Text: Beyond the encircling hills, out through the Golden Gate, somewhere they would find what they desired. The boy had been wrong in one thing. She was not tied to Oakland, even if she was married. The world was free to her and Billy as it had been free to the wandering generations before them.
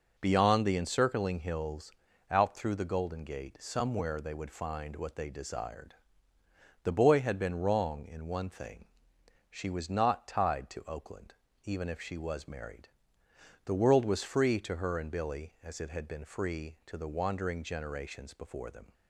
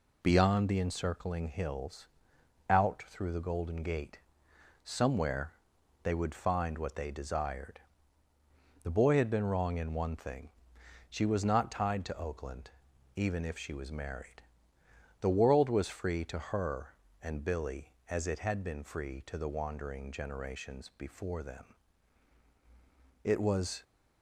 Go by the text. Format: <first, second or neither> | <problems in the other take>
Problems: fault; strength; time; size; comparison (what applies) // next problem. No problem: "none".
first | pauses between "somewhere" and "they"; noticeable; at 5.5 s; 0.50 s long // goes on to say "It was"; from 23.2 s on; 0.60 s long